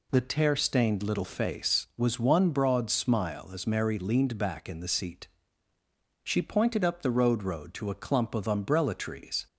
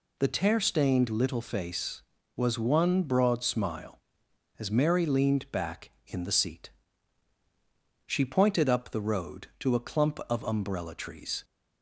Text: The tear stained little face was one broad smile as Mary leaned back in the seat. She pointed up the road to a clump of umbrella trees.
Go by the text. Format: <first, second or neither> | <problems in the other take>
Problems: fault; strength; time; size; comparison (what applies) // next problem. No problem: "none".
second | says "road" twice; at 7.4 s